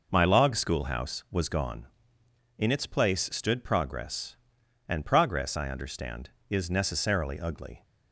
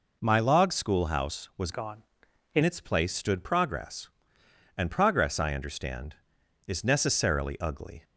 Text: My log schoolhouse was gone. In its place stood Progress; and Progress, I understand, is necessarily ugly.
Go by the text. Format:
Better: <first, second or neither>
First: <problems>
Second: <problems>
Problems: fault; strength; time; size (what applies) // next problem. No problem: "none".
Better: first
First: none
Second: changes voice from "gone" to "In"; from 1.7 to 2.6 s; 0.9 s long